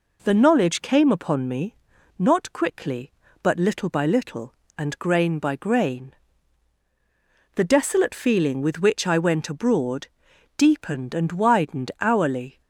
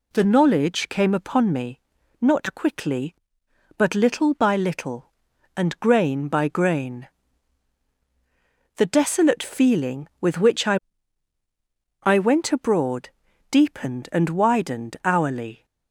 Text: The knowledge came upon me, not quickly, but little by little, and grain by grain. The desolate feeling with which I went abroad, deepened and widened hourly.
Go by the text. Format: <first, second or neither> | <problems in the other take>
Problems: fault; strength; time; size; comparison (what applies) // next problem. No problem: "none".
first | says "I" twice; at 12.0 s